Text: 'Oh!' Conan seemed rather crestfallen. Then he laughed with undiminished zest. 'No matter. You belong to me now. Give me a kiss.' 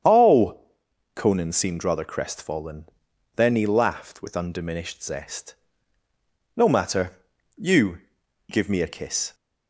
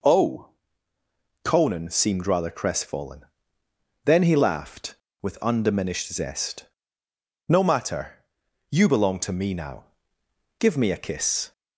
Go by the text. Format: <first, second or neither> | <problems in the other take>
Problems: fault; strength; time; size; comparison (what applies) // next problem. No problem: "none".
second | starts louder than the rest; strong; until 1.6 s; 8 dB // skips "belong to me now"; at 8.2 s